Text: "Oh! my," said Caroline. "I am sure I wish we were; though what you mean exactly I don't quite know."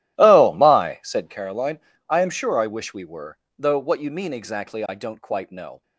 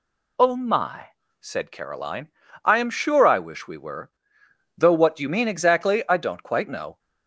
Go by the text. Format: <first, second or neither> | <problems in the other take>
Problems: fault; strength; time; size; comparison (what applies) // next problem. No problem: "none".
second | starts louder than the rest; strong; until 1.4 s; 14.5 dB